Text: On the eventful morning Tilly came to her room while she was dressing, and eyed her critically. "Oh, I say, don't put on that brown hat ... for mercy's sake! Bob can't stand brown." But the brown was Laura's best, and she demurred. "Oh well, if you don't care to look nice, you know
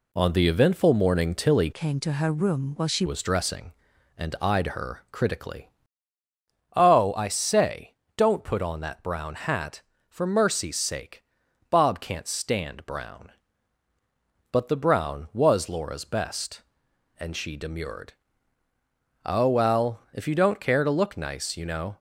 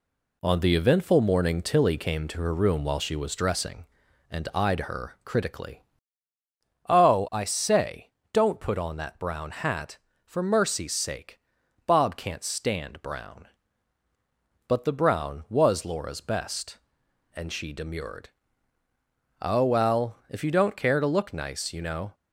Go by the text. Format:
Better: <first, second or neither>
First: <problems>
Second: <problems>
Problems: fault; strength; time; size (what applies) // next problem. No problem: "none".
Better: second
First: changes voice from "came" to "she"; from 1.7 to 3.0 s; 1.3 s long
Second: none